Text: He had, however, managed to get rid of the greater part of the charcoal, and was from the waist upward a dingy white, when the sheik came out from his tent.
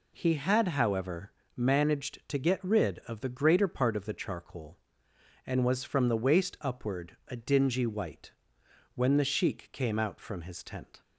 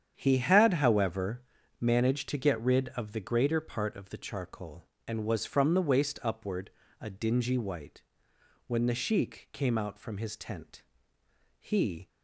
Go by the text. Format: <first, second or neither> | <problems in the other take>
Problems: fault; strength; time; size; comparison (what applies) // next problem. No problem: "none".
first | starts louder than the rest; strong; until 1.1 s; 8.5 dB // pauses between "upward" and "a"; slight; at 6.6 s; 0.32 s long // goes on to say "He"; slight; from 11.5 s on; 0.48 s long